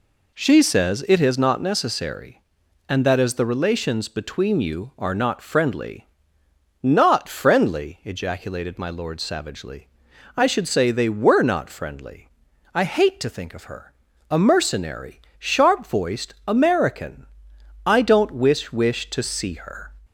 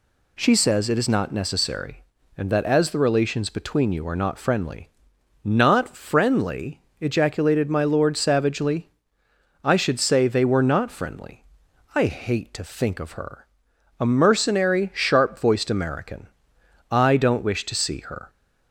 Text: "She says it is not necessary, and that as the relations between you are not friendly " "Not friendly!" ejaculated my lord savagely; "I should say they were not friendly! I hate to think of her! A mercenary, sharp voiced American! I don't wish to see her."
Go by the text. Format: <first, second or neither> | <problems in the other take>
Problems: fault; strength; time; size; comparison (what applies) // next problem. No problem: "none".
second | says "wish" twice; at 18.7 s